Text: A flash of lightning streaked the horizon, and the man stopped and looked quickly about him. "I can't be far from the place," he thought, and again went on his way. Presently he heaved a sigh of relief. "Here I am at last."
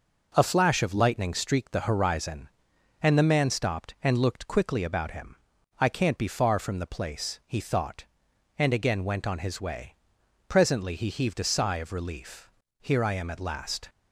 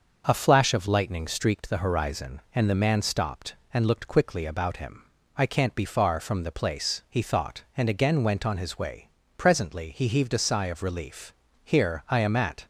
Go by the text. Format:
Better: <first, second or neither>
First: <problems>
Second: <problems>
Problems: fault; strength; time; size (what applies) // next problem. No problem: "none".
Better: first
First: none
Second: starts louder than the rest; until 1.2 s; 6.5 dB // stops before "last"; at 12.6 s